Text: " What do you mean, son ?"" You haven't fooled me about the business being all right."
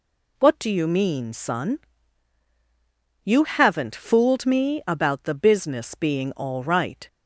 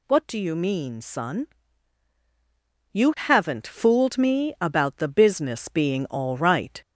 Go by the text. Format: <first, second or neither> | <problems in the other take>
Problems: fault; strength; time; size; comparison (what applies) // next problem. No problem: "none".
first | gets louder; strong; throughout; 13.5 dB